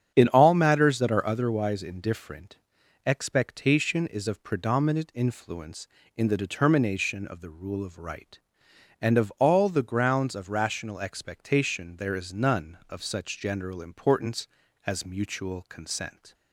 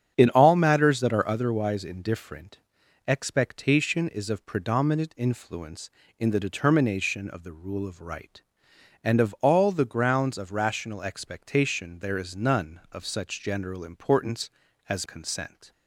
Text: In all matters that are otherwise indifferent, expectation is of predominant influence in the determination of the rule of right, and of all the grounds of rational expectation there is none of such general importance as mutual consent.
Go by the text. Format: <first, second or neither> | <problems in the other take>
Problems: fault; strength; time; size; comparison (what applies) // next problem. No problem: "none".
first | starts louder than the rest; strong; until 1.1 s; 8 dB; strong in the first // skips "mutual"; at 15.0 s